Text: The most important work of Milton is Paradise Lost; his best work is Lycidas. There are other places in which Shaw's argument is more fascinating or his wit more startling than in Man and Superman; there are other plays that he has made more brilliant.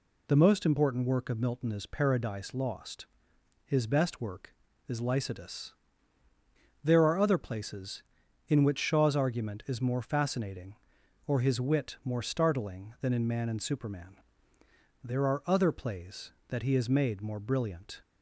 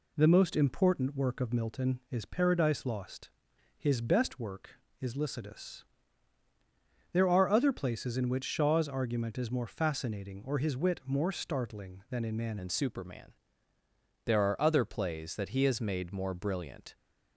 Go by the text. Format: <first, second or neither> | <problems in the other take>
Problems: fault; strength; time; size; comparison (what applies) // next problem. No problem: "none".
first | changes voice at "and"; from 12.5 s on; 4.4 s long